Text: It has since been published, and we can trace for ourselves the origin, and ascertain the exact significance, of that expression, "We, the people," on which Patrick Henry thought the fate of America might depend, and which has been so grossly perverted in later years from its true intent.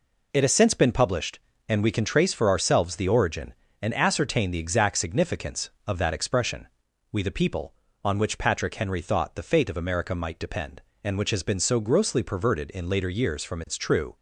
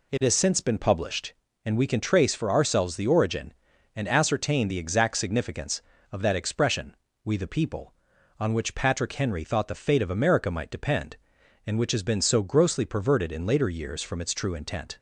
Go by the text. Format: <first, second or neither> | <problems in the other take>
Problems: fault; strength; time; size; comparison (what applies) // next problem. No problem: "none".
second | stops before "intent"; at 14.1 s